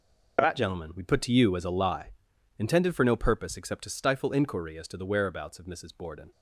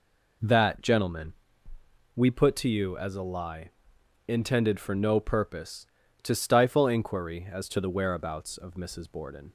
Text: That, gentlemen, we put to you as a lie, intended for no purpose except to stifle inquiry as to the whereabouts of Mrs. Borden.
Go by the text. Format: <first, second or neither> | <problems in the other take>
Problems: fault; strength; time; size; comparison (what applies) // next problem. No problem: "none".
first | skips "except"; at 6.0 s